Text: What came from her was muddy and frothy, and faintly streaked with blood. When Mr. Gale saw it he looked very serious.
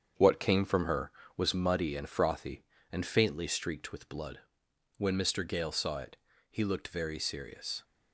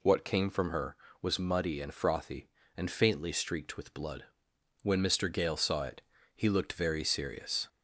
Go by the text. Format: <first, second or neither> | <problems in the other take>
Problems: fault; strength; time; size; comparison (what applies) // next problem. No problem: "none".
second | gets quieter; noticeable; throughout; 5.5 dB // pauses between "it" and "he"; slight; at 6.1 s; 0.34 s long; slight in the second